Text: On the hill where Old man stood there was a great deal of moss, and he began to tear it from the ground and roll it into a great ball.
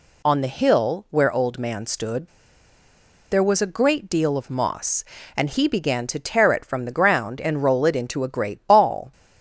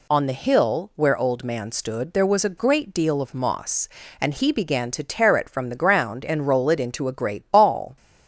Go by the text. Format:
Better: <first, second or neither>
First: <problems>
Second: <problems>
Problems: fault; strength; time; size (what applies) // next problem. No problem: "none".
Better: second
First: pauses between "stood" and "there"; at 2.2 s; 1.0 s long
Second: none